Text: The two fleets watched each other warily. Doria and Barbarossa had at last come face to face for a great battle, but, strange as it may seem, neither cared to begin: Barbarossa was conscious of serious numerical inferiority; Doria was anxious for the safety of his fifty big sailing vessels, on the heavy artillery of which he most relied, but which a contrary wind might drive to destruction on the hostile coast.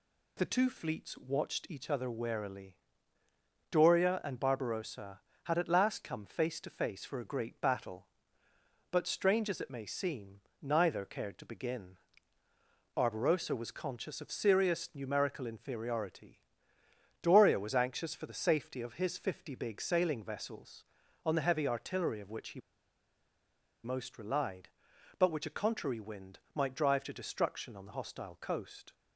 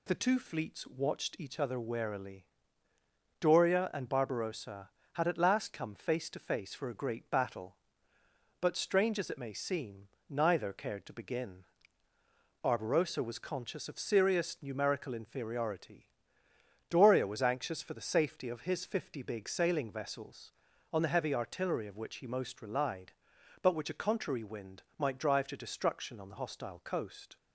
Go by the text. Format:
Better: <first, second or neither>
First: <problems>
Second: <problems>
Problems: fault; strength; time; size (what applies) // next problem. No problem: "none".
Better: second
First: pauses between "he" and "most"; at 22.5 s; 1.2 s long // pauses between "wind" and "might"; slight; at 26.3 s; 0.16 s long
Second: pauses between "wind" and "might"; slight; at 24.8 s; 0.16 s long